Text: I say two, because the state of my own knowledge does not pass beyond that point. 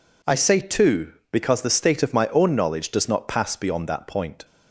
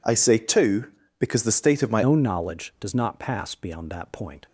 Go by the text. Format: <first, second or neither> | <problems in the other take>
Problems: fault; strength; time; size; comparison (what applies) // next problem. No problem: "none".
first | changes voice at "own"; from 2.0 s on; 2.4 s long